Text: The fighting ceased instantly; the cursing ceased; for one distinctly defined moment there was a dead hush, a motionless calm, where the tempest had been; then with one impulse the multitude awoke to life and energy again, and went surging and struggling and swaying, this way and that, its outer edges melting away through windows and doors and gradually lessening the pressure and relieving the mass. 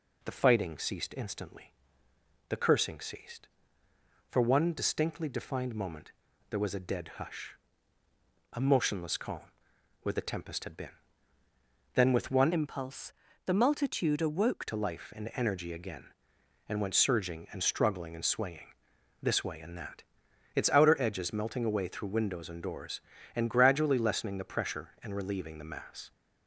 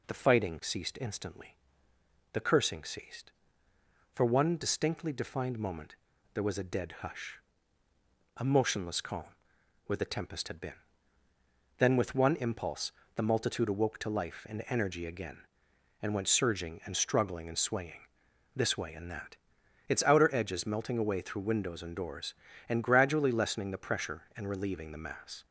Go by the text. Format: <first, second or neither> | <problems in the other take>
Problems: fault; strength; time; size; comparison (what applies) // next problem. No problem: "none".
second | pauses between "moment" and "there"; at 6.1 s; 0.40 s long; also in the second // changes voice from "impulse" to "awoke"; from 12.5 to 14.6 s; 2.1 s long // pauses between "impulse" and "the"; slight; at 13.1 s; 0.32 s long; slight in the second